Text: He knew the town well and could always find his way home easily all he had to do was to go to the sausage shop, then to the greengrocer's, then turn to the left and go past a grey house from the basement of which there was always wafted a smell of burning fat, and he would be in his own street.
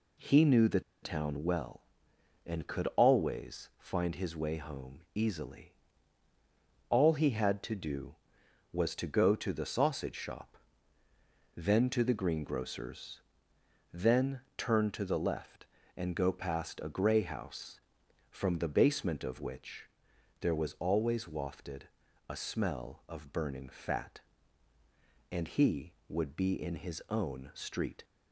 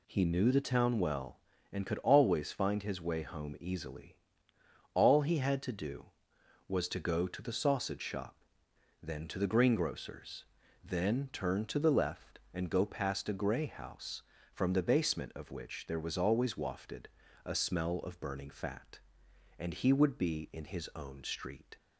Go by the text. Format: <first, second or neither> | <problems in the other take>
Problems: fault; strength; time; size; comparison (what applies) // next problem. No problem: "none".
second | pauses between "the" and "town"; slight; at 0.8 s; 0.21 s long // pauses between "easily" and "all"; at 5.7 s; 1.1 s long; noticeable in the second // pauses between "then" and "turn"; slight; at 14.3 s; 0.16 s long // pauses between "which" and "there"; noticeable; at 19.8 s; 0.56 s long // pauses between "wafted" and "a"; at 21.8 s; 0.40 s long; also in the second